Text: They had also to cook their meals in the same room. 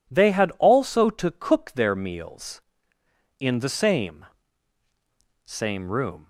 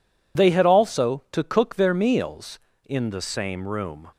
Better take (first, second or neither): second